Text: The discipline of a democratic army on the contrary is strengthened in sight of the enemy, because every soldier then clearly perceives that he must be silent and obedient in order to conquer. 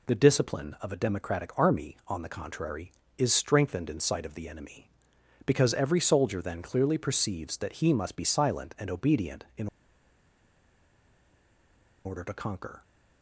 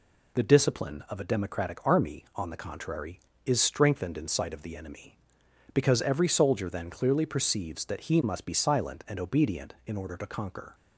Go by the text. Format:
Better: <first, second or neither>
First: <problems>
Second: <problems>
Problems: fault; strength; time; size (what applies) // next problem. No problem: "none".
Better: second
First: pauses between "in" and "order"; strong; at 9.6 s; 2.3 s long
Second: none